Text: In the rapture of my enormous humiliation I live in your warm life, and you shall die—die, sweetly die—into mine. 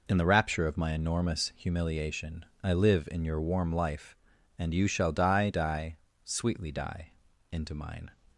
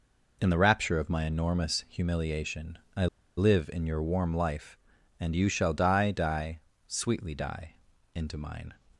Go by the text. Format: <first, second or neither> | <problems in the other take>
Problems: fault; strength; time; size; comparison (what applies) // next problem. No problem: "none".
first | pauses between "humiliation" and "I"; slight; at 2.7 s; 0.16 s long; slight in the first // pauses between "I" and "live"; slight; at 3.0 s; 0.30 s long